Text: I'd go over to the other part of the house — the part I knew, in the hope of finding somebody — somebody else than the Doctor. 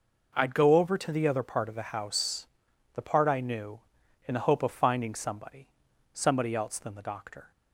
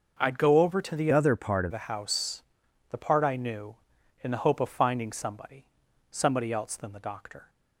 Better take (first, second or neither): first